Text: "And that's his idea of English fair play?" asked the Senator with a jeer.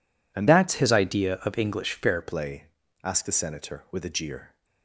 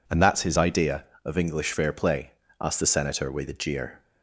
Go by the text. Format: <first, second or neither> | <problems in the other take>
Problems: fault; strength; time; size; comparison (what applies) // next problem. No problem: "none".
second | changes voice from "that's" to "fair"; from 0.4 to 2.2 s; 1.8 s long